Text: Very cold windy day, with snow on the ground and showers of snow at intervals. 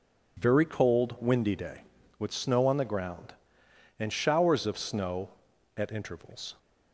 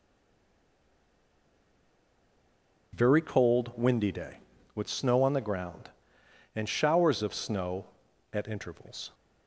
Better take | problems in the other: first | stays silent before the first word; strong; until 2.9 s; 2.9 s long

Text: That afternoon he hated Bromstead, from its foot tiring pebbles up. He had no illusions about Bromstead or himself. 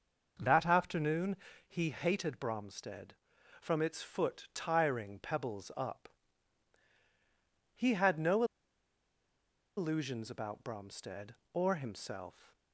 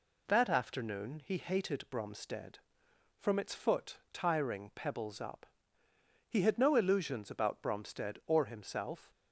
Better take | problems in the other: second | pauses between "afternoon" and "he"; slight; at 1.3 s; 0.32 s long // pauses between "no" and "illusions"; strong; at 8.4 s; 1.3 s long

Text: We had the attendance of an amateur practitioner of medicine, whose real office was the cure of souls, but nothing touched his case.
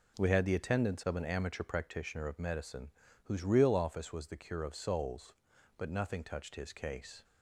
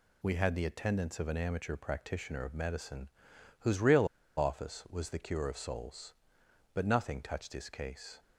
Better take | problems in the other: first | pauses between "real" and "office"; slight; at 4.0 s; 0.31 s long

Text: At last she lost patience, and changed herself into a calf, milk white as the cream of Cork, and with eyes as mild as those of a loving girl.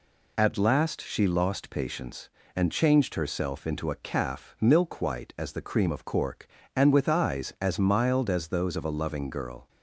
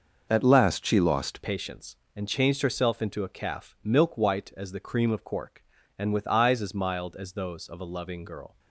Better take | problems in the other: first | changes voice at "patience"; from 1.4 s on; 7.1 s long

